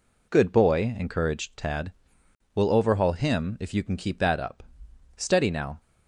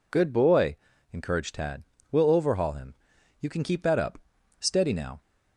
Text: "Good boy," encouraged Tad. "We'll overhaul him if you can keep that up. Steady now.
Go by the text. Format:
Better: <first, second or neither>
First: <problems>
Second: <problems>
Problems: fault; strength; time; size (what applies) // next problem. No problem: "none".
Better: first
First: none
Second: skips "if"; at 3.1 s